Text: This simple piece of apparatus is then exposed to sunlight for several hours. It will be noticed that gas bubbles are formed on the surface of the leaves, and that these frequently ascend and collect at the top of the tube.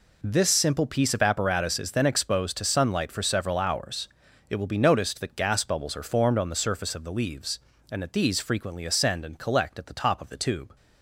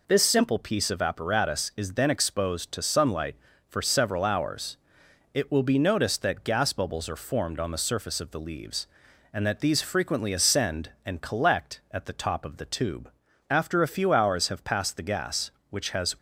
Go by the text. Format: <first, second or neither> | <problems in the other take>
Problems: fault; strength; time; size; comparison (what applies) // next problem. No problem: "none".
first | goes on to say "After a few hours have passed the gas which has"; strong; from 13.4 s on; 2.6 s long